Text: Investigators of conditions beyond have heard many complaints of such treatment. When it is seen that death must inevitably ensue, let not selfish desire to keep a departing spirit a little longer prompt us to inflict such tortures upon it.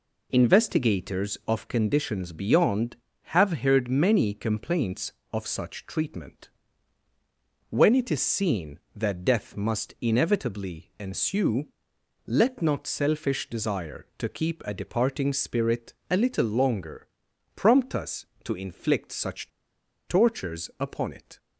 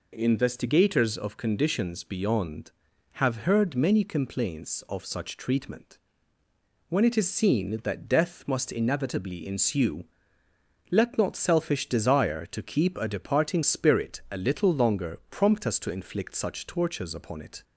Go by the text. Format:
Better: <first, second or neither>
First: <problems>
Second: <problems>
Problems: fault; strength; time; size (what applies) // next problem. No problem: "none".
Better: second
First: pauses between "spirit" and "a"; slight; at 15.9 s; 0.18 s long // pauses between "longer" and "prompt"; noticeable; at 17.0 s; 0.48 s long // pauses between "such" and "tortures"; noticeable; at 19.4 s; 0.57 s long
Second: none